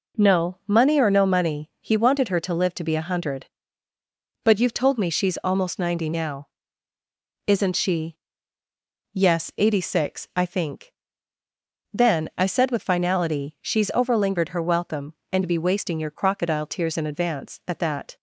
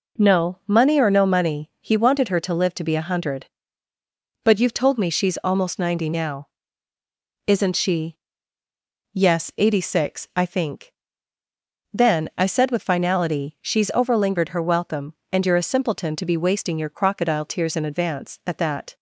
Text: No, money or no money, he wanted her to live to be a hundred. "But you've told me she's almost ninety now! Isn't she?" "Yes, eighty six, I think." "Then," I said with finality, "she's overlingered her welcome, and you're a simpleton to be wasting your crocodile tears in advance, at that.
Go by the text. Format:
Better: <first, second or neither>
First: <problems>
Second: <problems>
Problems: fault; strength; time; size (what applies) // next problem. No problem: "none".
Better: second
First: skips "you're a simpleton to"; at 15.4 s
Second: none